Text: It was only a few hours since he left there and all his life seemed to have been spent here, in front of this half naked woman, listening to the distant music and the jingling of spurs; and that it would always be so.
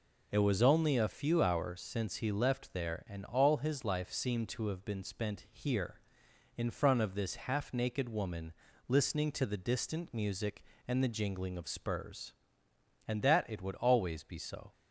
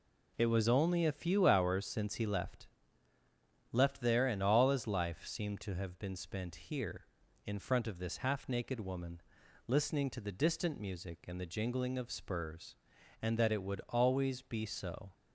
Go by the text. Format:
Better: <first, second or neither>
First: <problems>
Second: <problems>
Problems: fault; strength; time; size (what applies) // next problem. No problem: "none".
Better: first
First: none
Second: says "left" twice; at 3.6 s